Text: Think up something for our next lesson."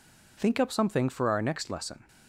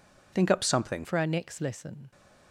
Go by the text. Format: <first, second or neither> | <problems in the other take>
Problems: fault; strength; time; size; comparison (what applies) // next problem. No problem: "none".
first | changes voice at "for"; from 1.0 s on; 1.1 s long